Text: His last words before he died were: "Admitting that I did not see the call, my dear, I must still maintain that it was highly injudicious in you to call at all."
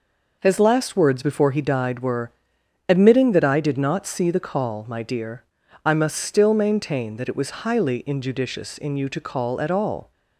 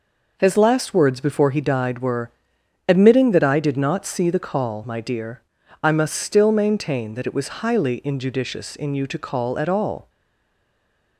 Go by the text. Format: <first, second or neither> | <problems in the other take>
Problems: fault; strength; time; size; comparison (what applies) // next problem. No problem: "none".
first | stays silent after the last word; from 10.0 s on; 1.1 s long